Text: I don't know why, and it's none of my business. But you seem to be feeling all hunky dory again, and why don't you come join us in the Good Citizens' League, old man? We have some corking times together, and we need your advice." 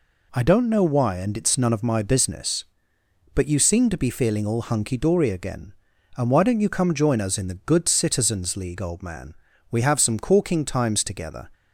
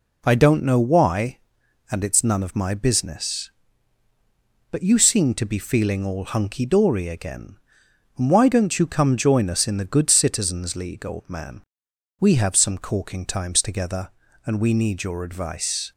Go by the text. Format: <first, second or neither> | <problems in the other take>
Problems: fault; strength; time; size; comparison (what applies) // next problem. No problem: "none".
second | stops before "and we need your advice"; at 11.5 s